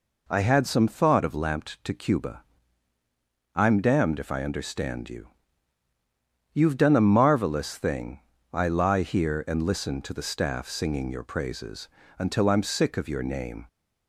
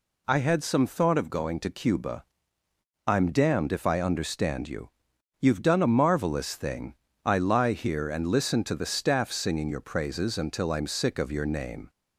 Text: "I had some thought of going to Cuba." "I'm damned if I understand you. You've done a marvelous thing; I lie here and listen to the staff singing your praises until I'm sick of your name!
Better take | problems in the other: second | says "lamped" for "going"; at 1.3 s // pauses between "praises" and "until"; slight; at 11.8 s; 0.30 s long

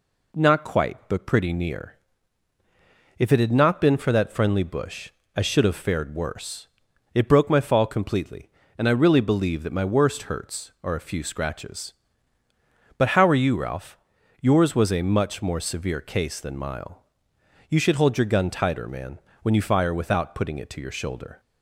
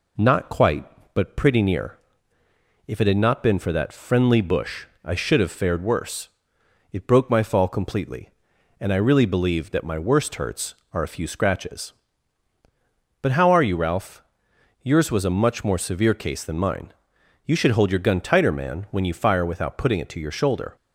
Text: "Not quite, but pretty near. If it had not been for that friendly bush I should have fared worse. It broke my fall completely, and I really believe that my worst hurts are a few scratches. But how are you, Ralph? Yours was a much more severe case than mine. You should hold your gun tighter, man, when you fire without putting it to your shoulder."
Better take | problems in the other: second | pauses between "bush" and "I"; slight; at 5.0 s; 0.26 s long; slight in the second // says "mile" for "mine"; at 16.5 s

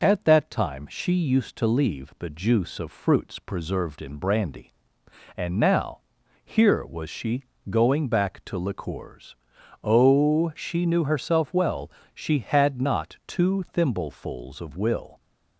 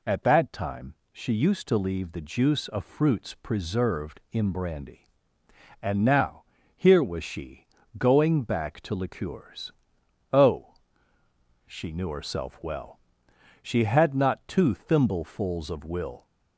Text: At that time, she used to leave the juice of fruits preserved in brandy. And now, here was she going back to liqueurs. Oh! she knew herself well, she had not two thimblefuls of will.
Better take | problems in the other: neither | pauses between "she" and "going"; slight; the same in both

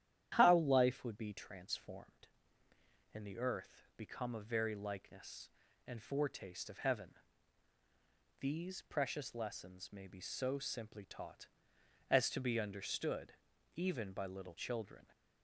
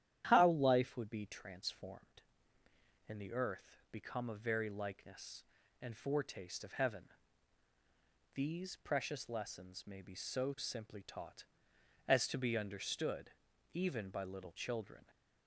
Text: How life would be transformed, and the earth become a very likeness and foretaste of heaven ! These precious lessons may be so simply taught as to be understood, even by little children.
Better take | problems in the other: neither | starts louder than the rest; strong; the same in both

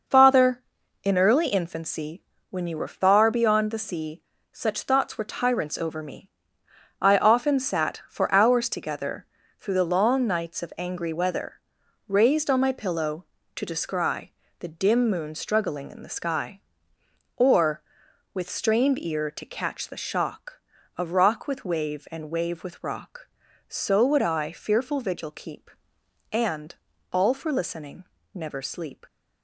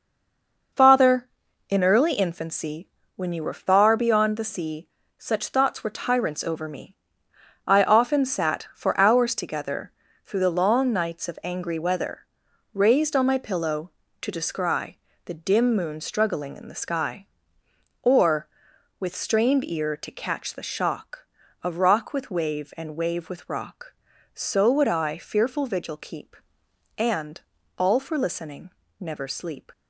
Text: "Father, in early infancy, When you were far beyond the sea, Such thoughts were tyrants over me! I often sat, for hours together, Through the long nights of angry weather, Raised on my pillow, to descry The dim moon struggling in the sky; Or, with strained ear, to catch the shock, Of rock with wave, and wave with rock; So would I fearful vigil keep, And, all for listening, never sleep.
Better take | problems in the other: first | stays silent before the first word; slight; until 0.7 s; 0.7 s long // pauses between "descry" and "The"; slight; at 14.9 s; 0.28 s long; slight in the first

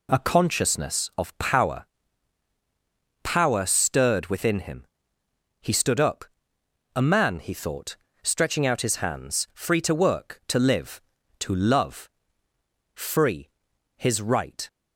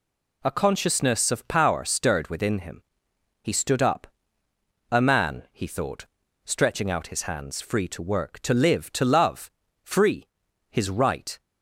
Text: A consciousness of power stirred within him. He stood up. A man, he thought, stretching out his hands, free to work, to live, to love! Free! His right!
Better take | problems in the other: second | says "power" twice; at 3.2 s

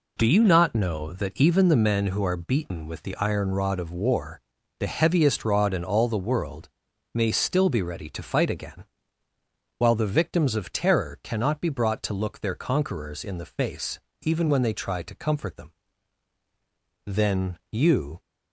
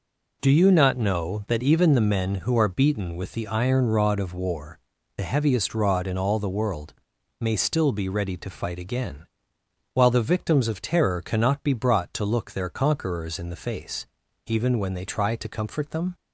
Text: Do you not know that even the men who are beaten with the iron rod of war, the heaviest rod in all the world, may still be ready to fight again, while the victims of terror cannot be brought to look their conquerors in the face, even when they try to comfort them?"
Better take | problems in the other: second | goes on to say "Then you"; noticeable; from 17.0 s on; 1.1 s long

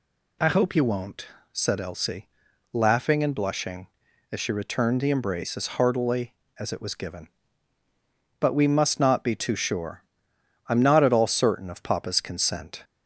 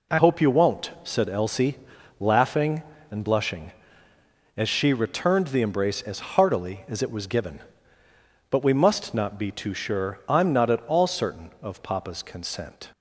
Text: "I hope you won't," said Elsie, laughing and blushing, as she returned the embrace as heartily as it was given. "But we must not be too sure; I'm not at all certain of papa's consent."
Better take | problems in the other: first | changes voice at "hope"; from 0.1 s on; 12.7 s long

